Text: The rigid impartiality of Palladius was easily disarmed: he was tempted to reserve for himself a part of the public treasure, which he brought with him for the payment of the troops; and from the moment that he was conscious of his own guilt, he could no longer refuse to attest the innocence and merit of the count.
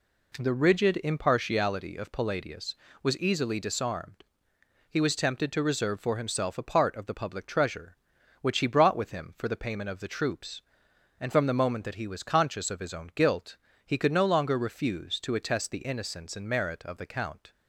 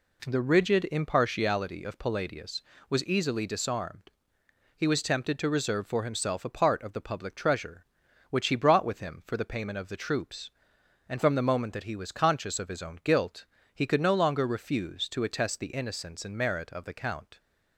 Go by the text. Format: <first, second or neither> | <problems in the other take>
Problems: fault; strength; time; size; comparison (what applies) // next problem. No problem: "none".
neither | none